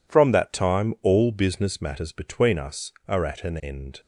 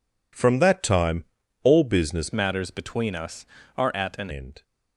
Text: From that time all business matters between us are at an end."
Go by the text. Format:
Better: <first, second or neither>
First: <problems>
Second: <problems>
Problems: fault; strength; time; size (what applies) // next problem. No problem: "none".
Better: first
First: none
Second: pauses between "time" and "all"; at 1.2 s; 0.38 s long // changes voice from "matters" to "an"; from 2.3 to 4.2 s; 1.9 s long